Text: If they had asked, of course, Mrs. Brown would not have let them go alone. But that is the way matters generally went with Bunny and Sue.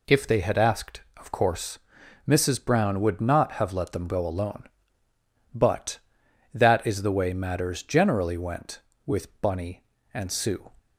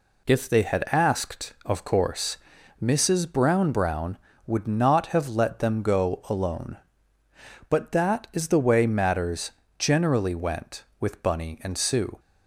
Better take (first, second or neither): first